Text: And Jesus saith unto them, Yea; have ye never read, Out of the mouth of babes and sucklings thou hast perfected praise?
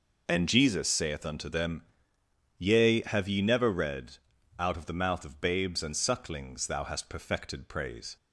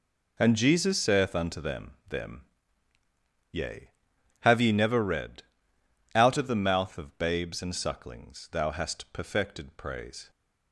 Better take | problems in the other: first | says "them" twice; at 2.0 s

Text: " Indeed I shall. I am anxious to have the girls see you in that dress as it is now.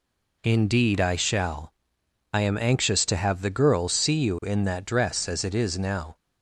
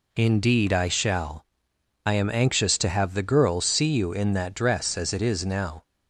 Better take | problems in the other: neither | none

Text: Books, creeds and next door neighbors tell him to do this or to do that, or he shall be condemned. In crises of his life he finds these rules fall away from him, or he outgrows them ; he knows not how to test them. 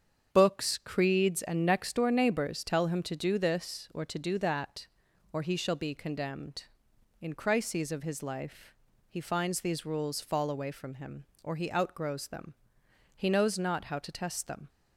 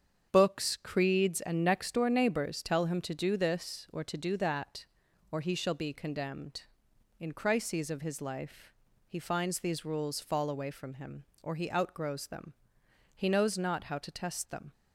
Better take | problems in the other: neither | starts louder than the rest; strong; the same in both // pauses between "life" and "he"; slight; the same in both

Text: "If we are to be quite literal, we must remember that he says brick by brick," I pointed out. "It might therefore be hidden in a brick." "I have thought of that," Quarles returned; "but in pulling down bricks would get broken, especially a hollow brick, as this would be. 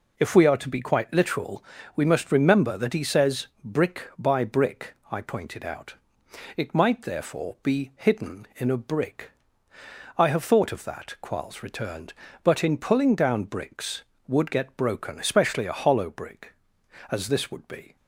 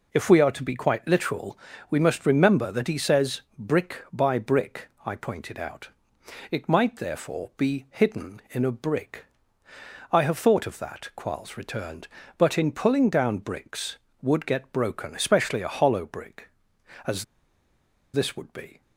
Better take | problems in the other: first | pauses between "as" and "this"; noticeable; at 17.2 s; 0.91 s long

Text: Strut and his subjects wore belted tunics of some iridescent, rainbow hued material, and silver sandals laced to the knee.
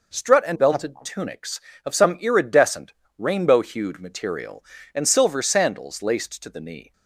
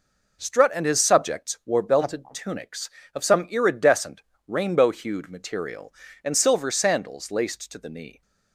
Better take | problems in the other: second | skips "his subjects wore"; at 0.5 s

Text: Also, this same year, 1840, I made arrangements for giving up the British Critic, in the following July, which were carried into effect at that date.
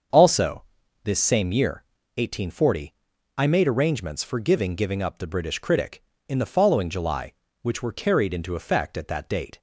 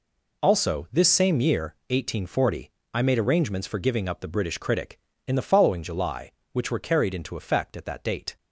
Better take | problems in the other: second | starts louder than the rest; until 1.5 s; 6.5 dB // says "giving" twice; at 4.7 s

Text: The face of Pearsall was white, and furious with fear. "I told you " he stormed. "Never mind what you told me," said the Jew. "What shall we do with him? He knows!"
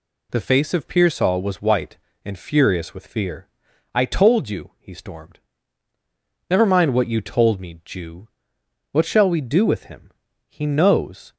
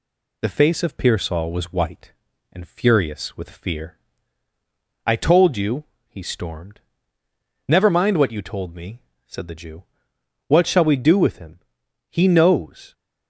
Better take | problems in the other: second | skips "said the"; at 7.8 s

